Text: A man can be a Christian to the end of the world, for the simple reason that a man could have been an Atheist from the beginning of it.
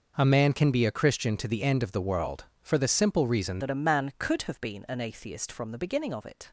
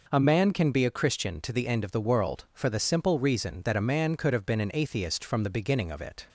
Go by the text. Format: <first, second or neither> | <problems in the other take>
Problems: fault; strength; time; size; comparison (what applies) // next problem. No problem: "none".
second | changes voice at "that"; from 3.5 s on; 3.0 s long